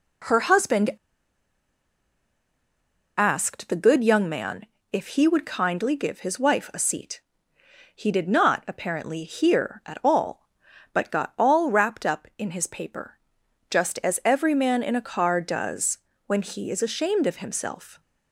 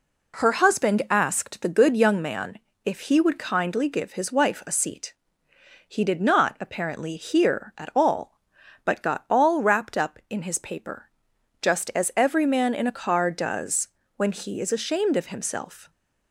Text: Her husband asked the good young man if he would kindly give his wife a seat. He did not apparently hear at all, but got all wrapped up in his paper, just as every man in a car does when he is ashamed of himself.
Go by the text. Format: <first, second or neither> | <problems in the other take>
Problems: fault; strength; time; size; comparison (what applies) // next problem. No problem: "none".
second | pauses between "husband" and "asked"; strong; at 0.9 s; 2.2 s long // pauses between "man" and "if"; slight; at 4.6 s; 0.28 s long; slight in the second // pauses between "does" and "when"; slight; at 15.9 s; 0.28 s long; slight in the second